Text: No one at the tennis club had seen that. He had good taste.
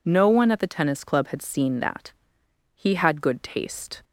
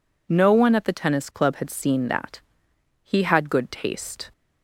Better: neither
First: none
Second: none

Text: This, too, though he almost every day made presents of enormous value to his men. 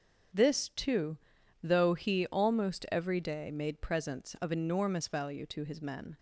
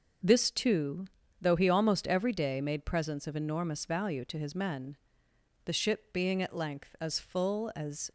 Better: first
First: starts louder than the rest; until 1.8 s; 7 dB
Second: starts louder than the rest; until 1.6 s; 6 dB // goes on to say "The ship being at length as full as"; strong; from 5.6 s on; 2.4 s long

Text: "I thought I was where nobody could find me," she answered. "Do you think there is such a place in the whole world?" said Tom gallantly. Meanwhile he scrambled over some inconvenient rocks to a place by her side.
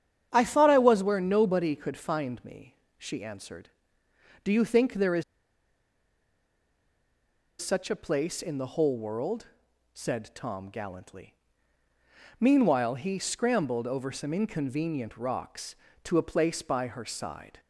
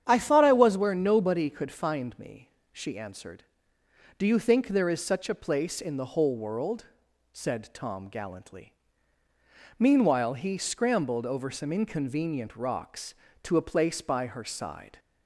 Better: second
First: starts louder than the rest; strong; until 1.3 s; 9 dB // pauses between "is" and "such"; strong; at 5.2 s; 2.3 s long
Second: starts louder than the rest; strong; until 1.0 s; 9 dB

